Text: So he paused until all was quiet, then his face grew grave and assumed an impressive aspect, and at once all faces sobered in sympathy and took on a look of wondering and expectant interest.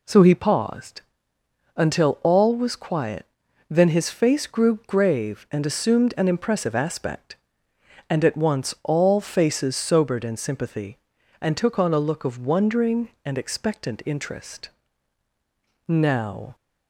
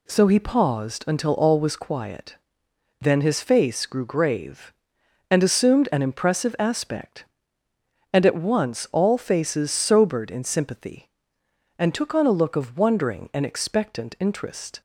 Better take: second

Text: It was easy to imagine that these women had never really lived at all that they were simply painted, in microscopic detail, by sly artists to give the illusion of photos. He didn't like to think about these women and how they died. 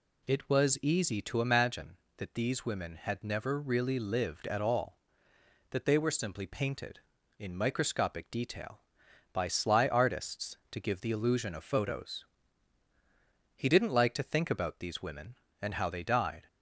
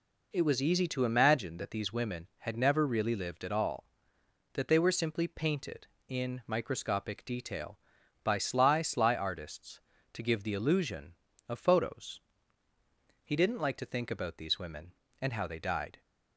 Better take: first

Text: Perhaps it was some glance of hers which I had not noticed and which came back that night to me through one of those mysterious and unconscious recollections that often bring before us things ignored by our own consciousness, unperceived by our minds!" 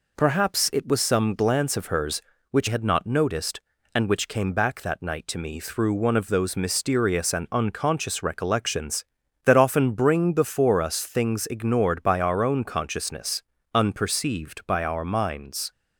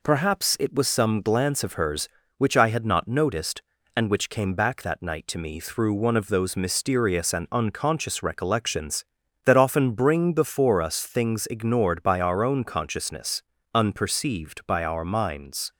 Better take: second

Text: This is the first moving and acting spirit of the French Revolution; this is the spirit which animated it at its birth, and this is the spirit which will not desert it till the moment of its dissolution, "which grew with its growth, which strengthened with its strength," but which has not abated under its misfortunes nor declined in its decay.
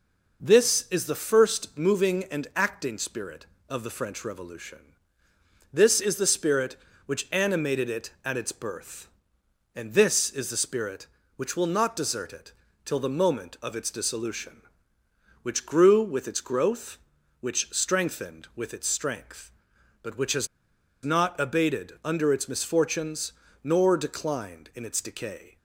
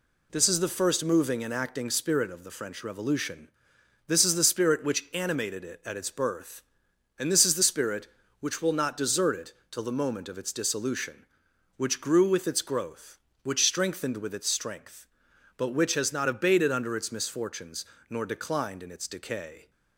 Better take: second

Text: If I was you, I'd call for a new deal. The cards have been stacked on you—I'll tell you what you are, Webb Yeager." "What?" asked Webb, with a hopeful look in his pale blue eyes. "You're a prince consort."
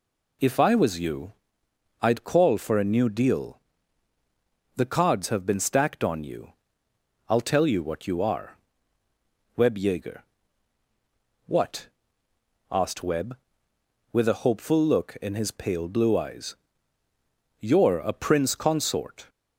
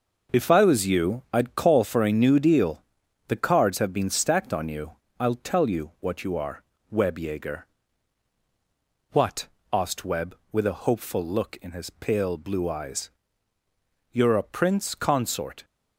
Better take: first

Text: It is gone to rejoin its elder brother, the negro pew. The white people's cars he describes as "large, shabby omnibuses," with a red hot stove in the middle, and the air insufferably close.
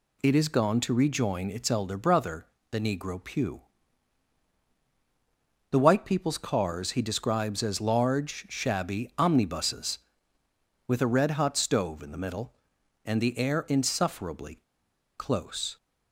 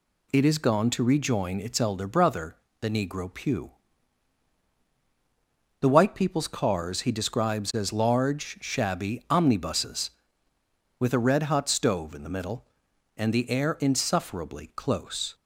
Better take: second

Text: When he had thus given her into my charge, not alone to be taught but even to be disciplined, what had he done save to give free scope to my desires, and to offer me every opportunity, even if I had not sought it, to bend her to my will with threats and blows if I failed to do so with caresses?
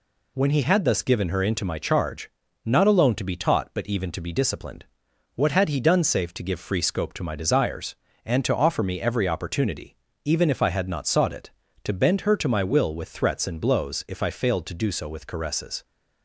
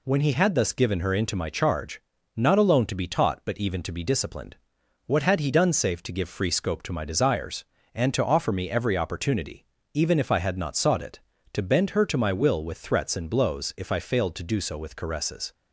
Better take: neither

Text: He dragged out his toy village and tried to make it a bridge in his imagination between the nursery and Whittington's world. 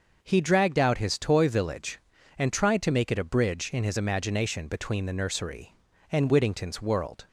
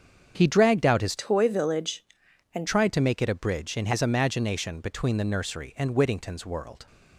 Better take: first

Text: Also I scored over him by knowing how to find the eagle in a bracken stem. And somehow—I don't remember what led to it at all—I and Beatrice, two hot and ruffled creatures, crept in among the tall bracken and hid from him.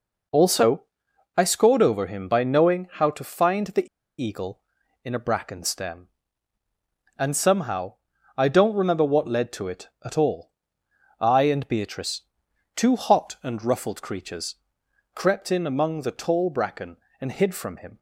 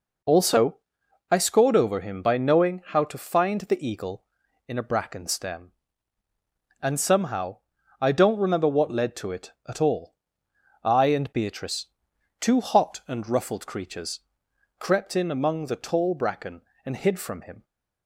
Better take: second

